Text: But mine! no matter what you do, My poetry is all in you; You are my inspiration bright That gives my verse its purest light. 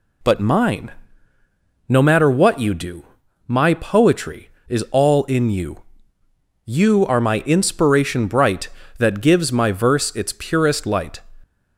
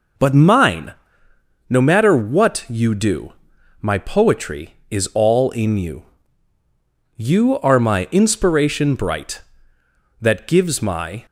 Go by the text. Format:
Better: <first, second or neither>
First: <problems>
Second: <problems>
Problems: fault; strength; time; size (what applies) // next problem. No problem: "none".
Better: first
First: none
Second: stops before "verse its purest light"; at 11.2 s